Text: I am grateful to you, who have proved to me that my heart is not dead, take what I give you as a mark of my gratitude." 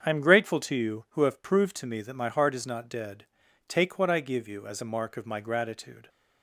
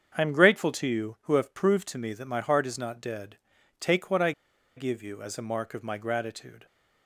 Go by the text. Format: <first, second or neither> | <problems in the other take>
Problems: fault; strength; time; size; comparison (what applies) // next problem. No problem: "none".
first | starts louder than the rest; strong; until 1.1 s; 7.5 dB; strong in the first // pauses between "I" and "give"; at 4.3 s; 0.45 s long